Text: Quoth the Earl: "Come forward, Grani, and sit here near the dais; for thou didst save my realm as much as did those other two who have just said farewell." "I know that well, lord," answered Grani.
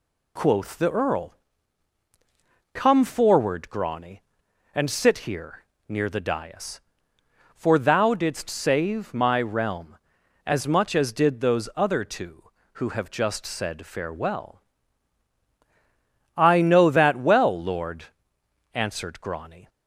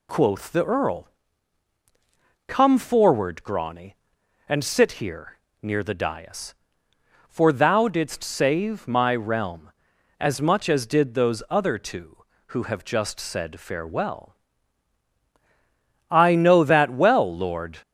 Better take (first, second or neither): first